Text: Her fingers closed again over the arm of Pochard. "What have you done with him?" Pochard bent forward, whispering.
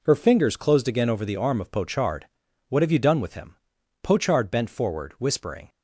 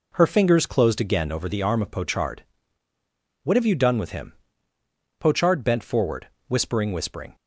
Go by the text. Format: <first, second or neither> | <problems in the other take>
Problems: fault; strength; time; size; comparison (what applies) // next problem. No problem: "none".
first | says "whispering" twice; at 6.9 s